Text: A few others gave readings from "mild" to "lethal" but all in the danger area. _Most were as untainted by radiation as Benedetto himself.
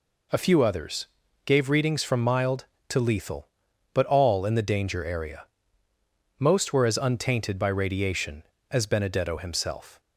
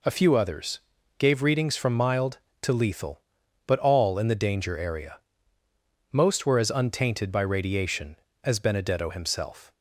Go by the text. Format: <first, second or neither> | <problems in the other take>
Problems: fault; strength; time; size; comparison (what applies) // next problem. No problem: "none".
neither | pauses between "others" and "gave"; the same in both